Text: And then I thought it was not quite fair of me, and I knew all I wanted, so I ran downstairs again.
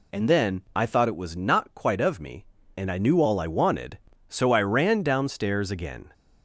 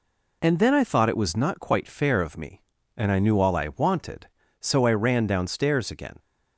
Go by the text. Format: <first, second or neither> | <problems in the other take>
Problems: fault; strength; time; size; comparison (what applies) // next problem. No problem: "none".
second | skips "fair"; at 2.0 s